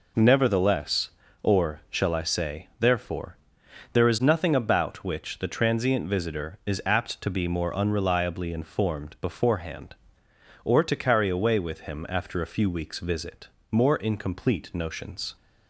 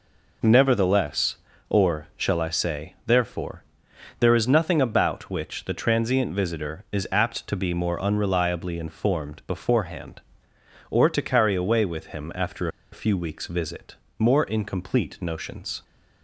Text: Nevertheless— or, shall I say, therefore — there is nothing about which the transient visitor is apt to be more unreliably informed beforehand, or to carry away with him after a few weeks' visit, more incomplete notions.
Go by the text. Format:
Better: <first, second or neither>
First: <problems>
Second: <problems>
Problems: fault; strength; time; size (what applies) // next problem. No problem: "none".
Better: first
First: none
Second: pauses between "after" and "a"; slight; at 12.6 s; 0.24 s long